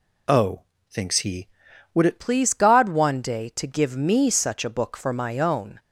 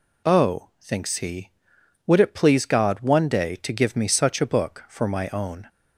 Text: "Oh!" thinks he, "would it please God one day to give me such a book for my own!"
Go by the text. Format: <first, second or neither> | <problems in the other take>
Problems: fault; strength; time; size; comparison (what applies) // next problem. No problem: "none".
second | changes voice at "please"; from 2.1 s on; 3.6 s long